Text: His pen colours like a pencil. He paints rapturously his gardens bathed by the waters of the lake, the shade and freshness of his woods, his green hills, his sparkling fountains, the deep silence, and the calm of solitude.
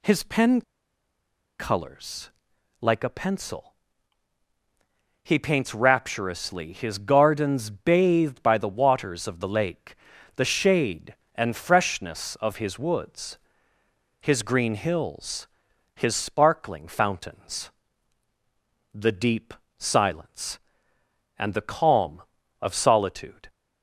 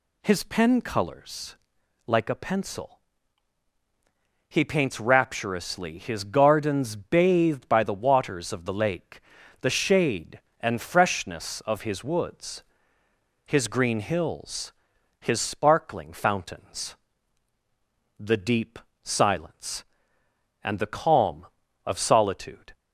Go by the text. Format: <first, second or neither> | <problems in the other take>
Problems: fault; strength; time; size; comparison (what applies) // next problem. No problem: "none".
second | pauses between "pen" and "colours"; noticeable; at 0.6 s; 0.96 s long // pauses between "colours" and "like"; noticeable; at 2.2 s; 0.50 s long; noticeable in the second // pauses between "deep" and "silence"; slight; at 19.5 s; 0.24 s long; slight in the second